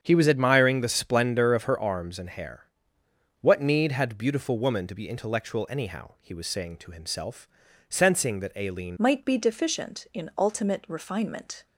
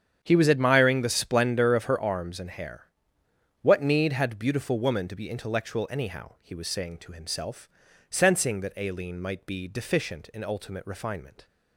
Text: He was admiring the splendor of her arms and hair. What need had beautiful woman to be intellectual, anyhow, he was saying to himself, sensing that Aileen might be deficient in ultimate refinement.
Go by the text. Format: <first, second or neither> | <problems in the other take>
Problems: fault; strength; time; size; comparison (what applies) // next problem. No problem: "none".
second | starts louder than the rest; strong; until 1.0 s; 7.5 dB; strong in the second // changes voice at "might"; from 8.9 s on; 2.7 s long